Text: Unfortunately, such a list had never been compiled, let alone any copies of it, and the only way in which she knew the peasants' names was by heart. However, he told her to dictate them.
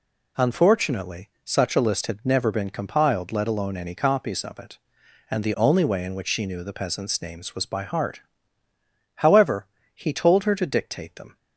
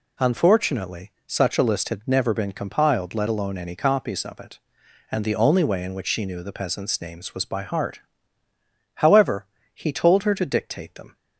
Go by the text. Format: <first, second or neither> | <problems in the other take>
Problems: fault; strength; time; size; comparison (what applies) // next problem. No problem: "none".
neither | none